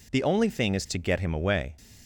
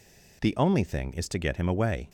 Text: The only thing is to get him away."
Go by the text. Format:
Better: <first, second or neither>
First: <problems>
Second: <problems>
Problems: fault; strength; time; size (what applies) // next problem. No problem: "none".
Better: neither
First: none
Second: none